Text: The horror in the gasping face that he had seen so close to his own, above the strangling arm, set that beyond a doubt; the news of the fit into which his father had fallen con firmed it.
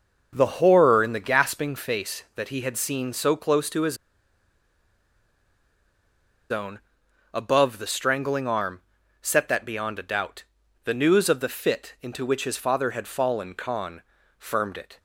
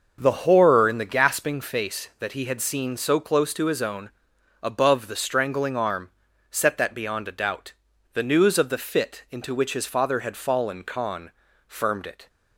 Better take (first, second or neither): second